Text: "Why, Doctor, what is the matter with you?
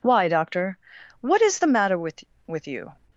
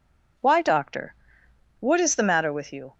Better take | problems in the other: second | says "with" twice; at 2.4 s

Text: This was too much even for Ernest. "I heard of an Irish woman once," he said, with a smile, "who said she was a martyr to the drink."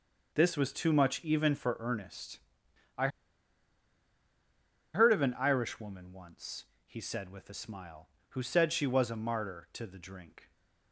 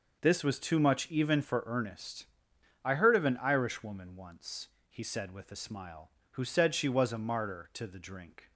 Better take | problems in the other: second | pauses between "I" and "heard"; strong; at 3.0 s; 1.8 s long

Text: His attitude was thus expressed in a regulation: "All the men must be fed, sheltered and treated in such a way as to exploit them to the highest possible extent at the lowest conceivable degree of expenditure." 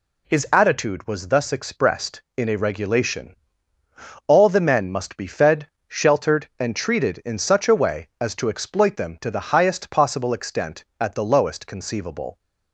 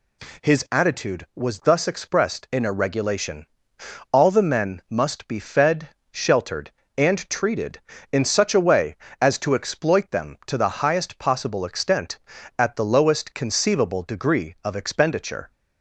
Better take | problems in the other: second | stops before "degree of expenditure"; at 12.3 s

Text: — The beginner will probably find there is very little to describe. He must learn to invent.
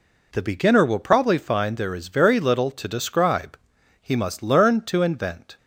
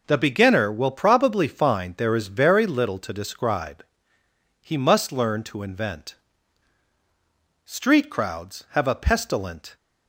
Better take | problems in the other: first | goes on to say "Street crowds have a pestilent"; strong; from 7.6 s on; 2.1 s long

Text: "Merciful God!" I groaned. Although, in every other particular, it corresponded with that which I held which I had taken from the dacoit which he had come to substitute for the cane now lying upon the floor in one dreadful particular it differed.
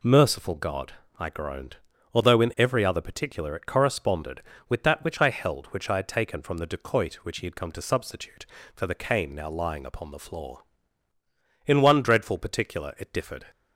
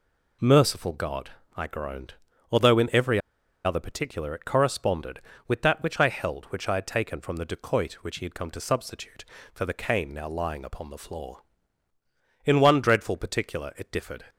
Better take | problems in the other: first | pauses between "every" and "other"; noticeable; at 3.1 s; 0.46 s long

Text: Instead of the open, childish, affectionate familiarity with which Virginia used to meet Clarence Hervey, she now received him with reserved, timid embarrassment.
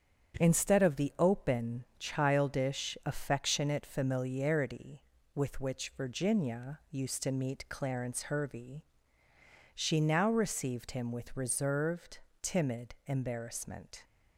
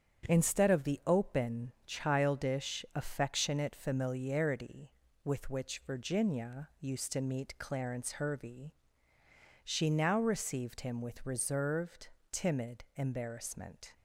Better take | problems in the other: neither | starts louder than the rest; strong; the same in both

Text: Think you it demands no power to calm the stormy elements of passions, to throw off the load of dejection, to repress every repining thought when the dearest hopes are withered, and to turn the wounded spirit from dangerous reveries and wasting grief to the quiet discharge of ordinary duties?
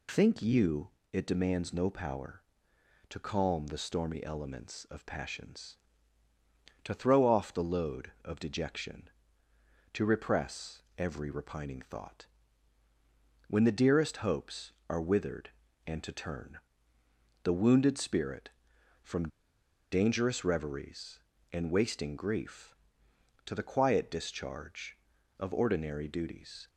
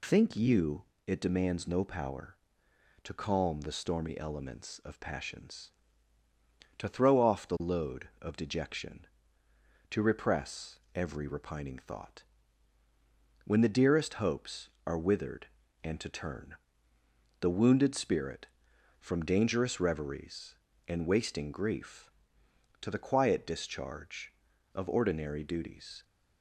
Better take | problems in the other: second | pauses between "you" and "it"; slight; at 0.8 s; 0.22 s long; slight in the second // pauses between "repress" and "every"; slight; at 10.8 s; 0.16 s long; slight in the second // pauses between "thought" and "when"; at 12.2 s; 1.2 s long; also in the second // pauses between "turn" and "the"; noticeable; at 16.5 s; 0.86 s long; noticeable in the second // pauses between "from" and "dangerous"; noticeable; at 19.2 s; 0.64 s long

